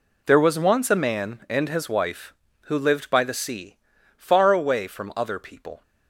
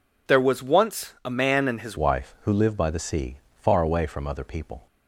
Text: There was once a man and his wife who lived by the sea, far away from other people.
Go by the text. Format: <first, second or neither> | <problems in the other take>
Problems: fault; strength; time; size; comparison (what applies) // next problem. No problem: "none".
first | changes voice at "wife"; from 1.9 s on; 2.9 s long